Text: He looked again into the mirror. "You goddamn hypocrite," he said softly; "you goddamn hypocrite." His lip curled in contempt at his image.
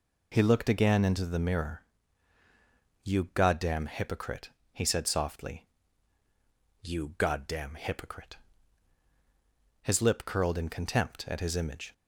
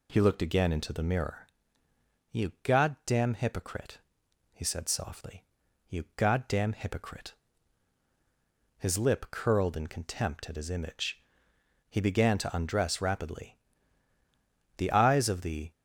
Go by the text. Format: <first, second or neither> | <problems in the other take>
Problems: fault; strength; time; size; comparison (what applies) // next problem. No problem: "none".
first | goes on to say "He began to undress rapidly The eyes of the"; strong; from 11.8 s on; 3.8 s long